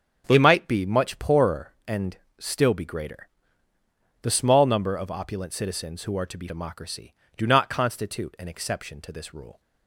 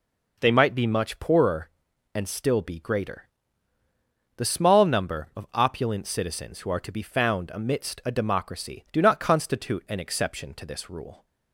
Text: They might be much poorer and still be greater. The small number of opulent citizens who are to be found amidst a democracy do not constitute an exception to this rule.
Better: second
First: starts louder than the rest; strong; until 1.3 s; 8 dB // pauses between "and" and "still"; slight; at 2.1 s; 0.22 s long // skips "found amidst a"; at 6.4 s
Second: none

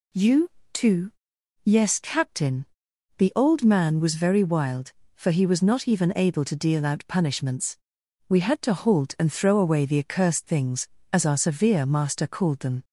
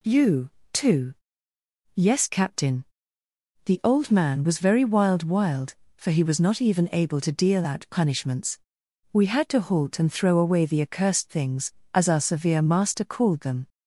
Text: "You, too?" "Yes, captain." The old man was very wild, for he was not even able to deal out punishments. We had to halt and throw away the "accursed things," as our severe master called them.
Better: first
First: none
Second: says "wild" twice; at 5.2 s

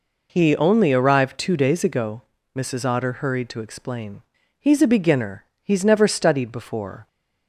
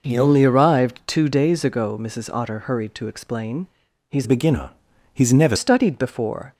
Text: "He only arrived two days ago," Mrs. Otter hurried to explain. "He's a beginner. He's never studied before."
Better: first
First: none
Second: changes voice from "a" to "never"; from 4.2 to 5.5 s; 1.3 s long

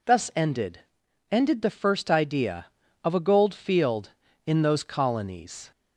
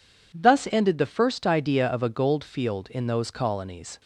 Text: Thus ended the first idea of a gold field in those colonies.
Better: second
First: says "ended" twice; at 1.3 s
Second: none

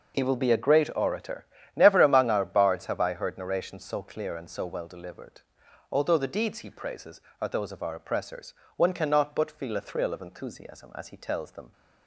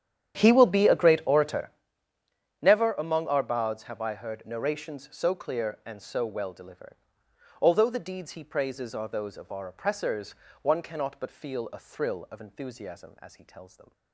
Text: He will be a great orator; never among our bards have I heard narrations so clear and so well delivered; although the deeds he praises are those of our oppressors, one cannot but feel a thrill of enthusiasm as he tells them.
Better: first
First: none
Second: starts louder than the rest; strong; until 1.8 s; 9.5 dB

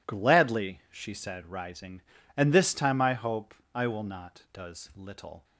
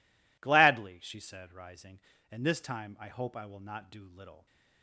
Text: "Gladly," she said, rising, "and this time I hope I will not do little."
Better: second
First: pauses between "hope" and "I"; slight; at 3.5 s; 0.20 s long // says "does" for "do"; at 4.5 s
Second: none

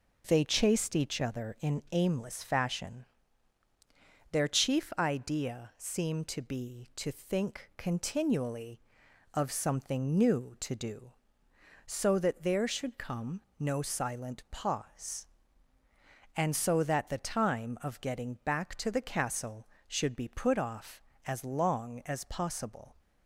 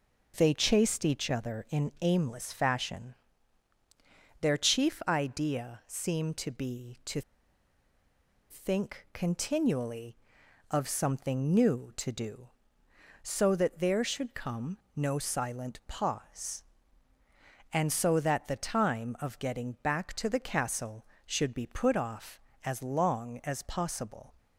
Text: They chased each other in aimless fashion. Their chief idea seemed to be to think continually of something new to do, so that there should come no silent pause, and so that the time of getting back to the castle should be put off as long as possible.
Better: first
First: pauses between "come" and "no"; slight; at 13.4 s; 0.18 s long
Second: pauses between "to" and "think"; strong; at 7.2 s; 1.2 s long // pauses between "come" and "no"; slight; at 14.7 s; 0.18 s long

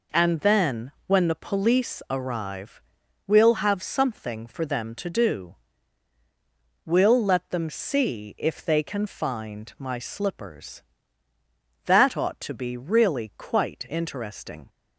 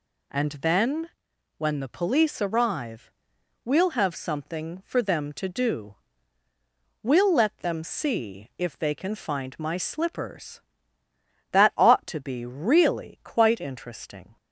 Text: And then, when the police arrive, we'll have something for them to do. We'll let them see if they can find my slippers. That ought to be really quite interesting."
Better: neither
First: none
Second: none

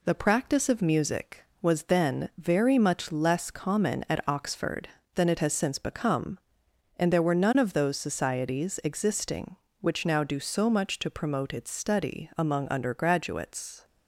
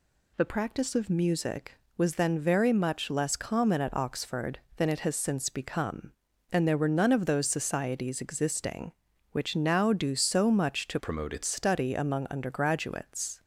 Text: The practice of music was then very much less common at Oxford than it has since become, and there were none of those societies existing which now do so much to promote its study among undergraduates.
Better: first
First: none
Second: changes voice from "promote" to "its"; from 10.9 to 11.4 s; 0.5 s long

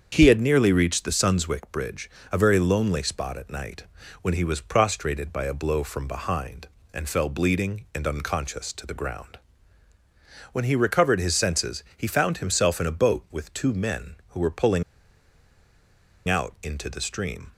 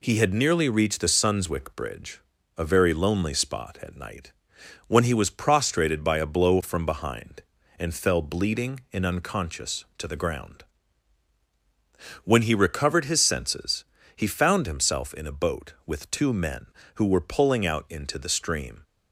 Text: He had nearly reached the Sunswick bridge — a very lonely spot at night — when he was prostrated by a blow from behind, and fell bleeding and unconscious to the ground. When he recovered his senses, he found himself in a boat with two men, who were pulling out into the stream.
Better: second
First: starts louder than the rest; strong; until 1.1 s; 7 dB // pauses between "pulling" and "out"; strong; at 14.8 s; 1.4 s long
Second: none

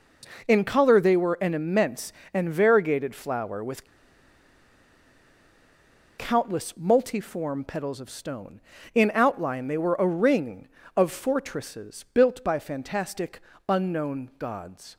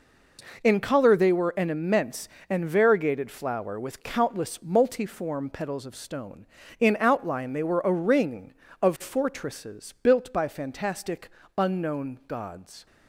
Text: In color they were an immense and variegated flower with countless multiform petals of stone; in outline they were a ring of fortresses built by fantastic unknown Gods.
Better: second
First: pauses between "with" and "countless"; strong; at 3.8 s; 2.3 s long // pauses between "fantastic" and "unknown"; slight; at 13.4 s; 0.28 s long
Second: pauses between "fantastic" and "unknown"; slight; at 11.2 s; 0.28 s long

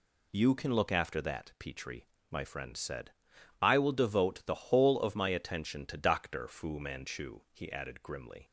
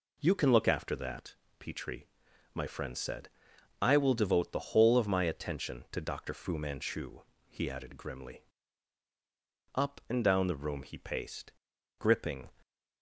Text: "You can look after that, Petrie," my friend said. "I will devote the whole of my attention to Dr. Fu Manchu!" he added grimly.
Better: first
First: none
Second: goes on to say "Up and down the room he paced gripping"; strong; from 9.7 s on; 2.7 s long

